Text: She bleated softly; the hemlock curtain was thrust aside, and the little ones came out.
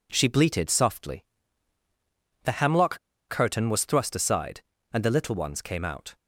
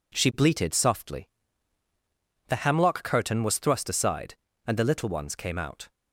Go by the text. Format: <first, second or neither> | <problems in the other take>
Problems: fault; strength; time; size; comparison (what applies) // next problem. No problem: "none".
second | pauses between "hemlock" and "curtain"; slight; at 2.9 s; 0.30 s long